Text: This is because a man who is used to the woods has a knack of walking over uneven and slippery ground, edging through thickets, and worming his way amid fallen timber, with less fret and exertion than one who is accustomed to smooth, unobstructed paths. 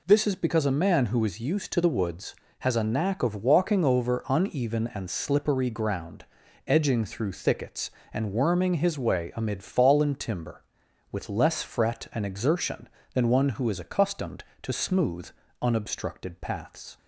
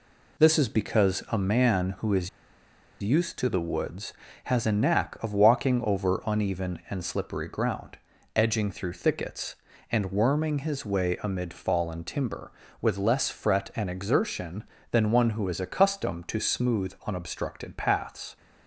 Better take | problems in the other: first | pauses between "is" and "used"; noticeable; at 2.2 s; 0.71 s long

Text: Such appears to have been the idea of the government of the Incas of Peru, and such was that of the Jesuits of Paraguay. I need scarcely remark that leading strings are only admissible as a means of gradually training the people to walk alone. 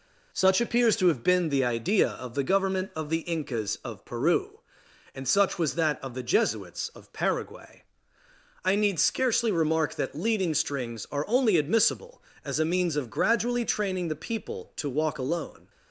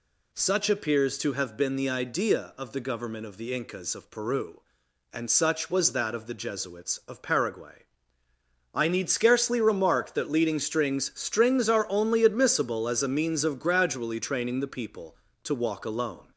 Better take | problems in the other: first | says "strings" twice; at 11.1 s

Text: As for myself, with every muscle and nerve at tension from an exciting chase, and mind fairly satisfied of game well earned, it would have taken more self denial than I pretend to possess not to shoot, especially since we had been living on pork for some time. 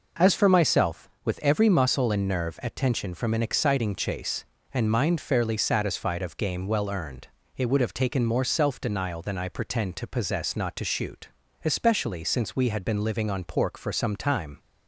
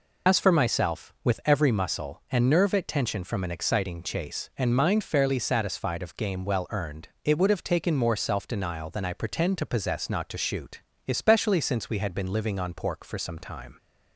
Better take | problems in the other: first | loses the start of "As"; at 0.2 s; 95 ms

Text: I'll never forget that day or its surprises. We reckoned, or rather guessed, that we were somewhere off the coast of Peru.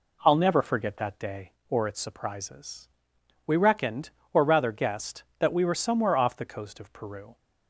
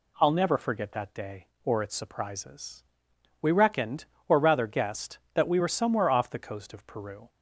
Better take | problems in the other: second | starts louder than the rest; slight; until 1.6 s; 3 dB

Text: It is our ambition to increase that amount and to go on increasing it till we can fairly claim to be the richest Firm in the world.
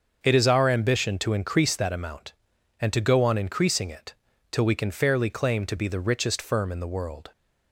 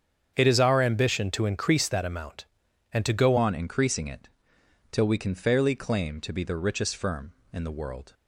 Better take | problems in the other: first | starts louder than the rest; strong; until 1.3 s; 7.5 dB; also in the first // changes voice at "on"; from 3.3 s on; 4.8 s long // pauses between "it" and "till"; noticeable; at 4.2 s; 0.64 s long; also in the first

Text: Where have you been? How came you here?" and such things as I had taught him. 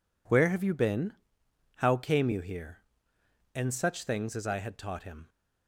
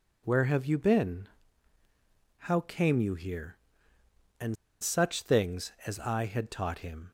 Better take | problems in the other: first | pauses between "and" and "such"; slight; at 4.5 s; 0.26 s long

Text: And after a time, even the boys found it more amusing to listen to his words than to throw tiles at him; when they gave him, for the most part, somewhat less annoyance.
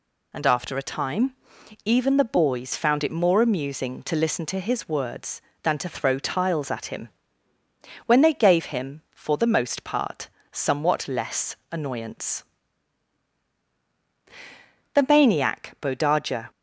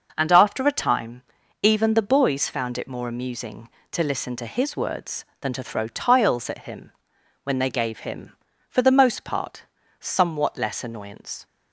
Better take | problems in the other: second | goes on to say "The maniac Bodaja"; from 14.9 s on; 1.5 s long

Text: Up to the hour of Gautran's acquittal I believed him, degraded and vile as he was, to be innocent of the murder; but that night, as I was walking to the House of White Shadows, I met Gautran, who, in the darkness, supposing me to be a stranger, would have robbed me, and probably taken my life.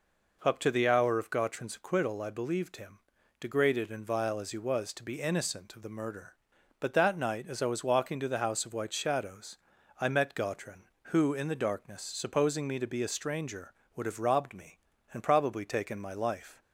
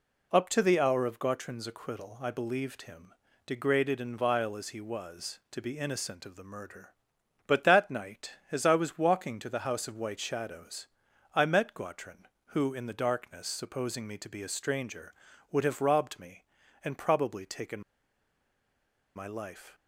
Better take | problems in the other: first | pauses between "taken" and "my"; strong; at 17.8 s; 1.3 s long

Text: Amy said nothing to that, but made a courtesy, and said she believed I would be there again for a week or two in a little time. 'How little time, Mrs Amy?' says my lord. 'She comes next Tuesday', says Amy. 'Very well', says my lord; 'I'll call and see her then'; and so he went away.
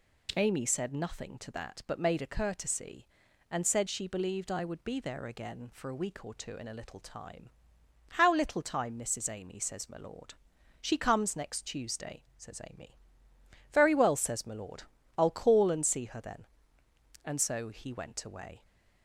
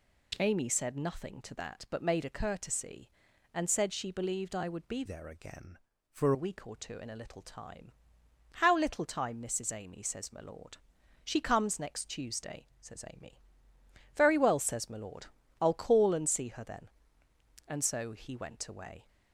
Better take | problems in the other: first | changes voice from "there" to "for"; from 5.0 to 6.3 s; 1.3 s long

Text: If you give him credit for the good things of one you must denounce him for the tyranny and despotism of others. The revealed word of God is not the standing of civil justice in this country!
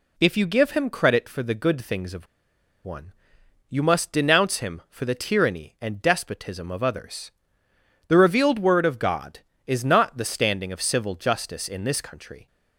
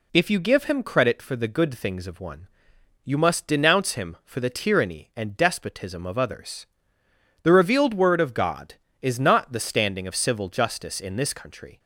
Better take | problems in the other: second | pauses between "of" and "one"; noticeable; at 2.2 s; 0.58 s long // pauses between "one" and "you"; noticeable; at 3.1 s; 0.58 s long; noticeable in the second

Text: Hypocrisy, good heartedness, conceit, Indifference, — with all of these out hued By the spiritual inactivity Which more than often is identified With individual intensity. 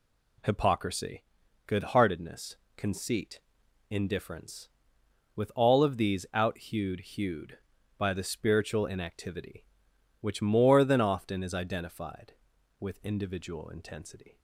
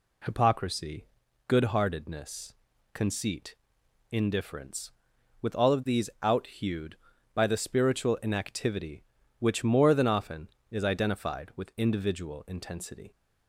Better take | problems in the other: second | says "hued" twice; at 6.9 s

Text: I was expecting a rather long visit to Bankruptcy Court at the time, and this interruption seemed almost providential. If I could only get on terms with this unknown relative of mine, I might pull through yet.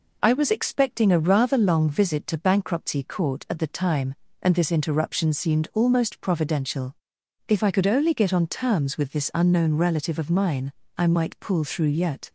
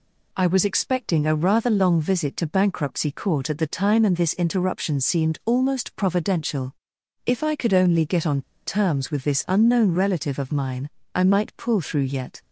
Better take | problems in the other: first | pauses between "on" and "terms"; slight; at 8.4 s; 0.25 s long

